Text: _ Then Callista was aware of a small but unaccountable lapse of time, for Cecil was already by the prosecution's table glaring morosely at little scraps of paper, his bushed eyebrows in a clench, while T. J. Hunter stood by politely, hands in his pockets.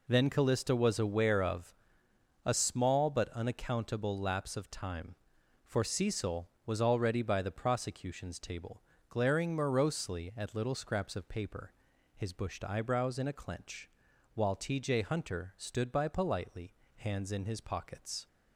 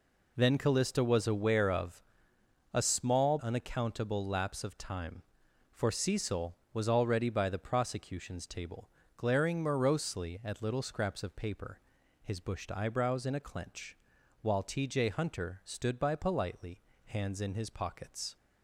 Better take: first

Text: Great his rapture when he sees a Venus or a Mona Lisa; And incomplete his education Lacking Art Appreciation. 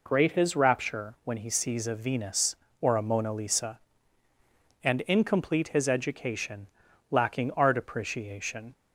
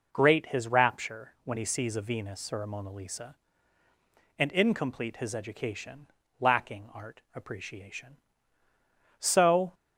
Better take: first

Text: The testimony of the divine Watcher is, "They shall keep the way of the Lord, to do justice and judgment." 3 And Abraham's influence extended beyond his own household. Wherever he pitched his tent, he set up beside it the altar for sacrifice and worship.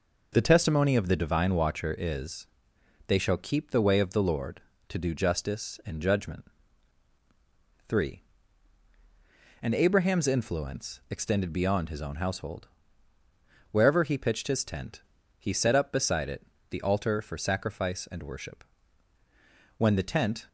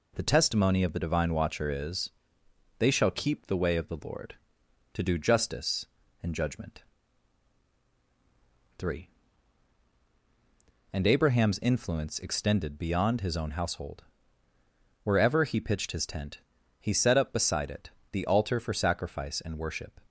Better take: second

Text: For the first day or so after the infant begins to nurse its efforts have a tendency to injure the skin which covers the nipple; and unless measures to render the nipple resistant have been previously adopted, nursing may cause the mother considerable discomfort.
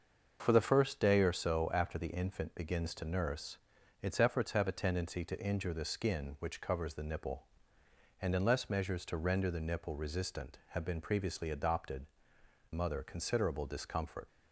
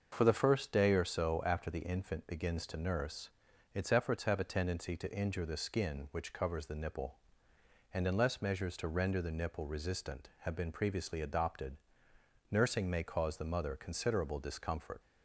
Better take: second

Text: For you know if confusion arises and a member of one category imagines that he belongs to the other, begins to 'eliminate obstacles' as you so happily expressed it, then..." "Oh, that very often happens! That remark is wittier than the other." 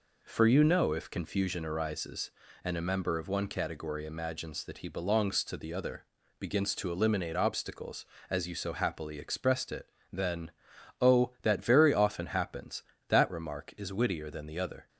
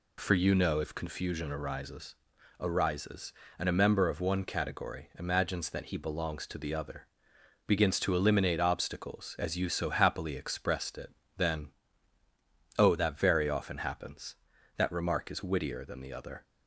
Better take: first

